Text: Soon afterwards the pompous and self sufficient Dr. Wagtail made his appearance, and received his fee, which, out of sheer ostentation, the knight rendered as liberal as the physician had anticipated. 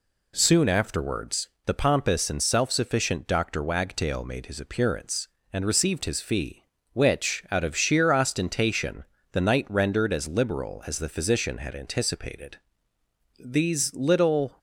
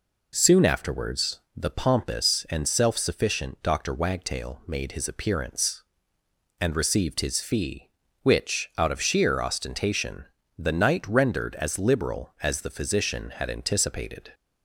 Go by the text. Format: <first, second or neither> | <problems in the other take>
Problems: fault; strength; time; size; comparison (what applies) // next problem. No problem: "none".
second | pauses between "afterwards" and "the"; slight; at 1.4 s; 0.18 s long; slight in the second // goes on to say "These little"; noticeable; from 13.3 s on; 1.2 s long